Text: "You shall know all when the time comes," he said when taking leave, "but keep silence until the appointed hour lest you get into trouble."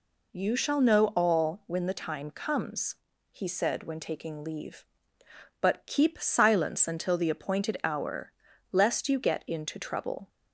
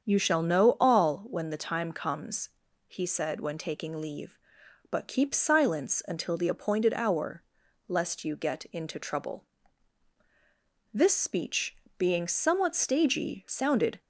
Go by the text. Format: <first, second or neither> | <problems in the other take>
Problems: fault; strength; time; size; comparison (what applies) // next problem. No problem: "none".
first | starts louder than the rest; strong; until 1.0 s; 7.5 dB // pauses between "hour" and "lest"; at 7.4 s; 0.44 s long; slight in the first // goes on to say "This speech being somewhat stagey sounded"; strong; from 10.9 s on; 3.0 s long